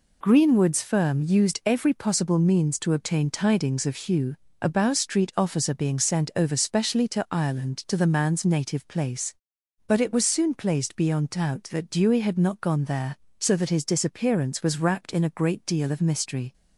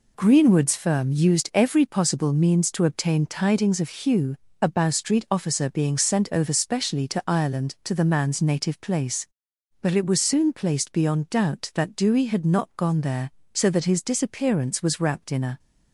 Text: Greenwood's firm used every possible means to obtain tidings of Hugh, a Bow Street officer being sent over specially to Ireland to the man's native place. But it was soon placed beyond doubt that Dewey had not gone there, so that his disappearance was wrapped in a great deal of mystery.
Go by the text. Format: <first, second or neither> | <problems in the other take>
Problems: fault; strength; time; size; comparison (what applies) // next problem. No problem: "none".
first | stops before "great deal of mystery"; at 15.5 s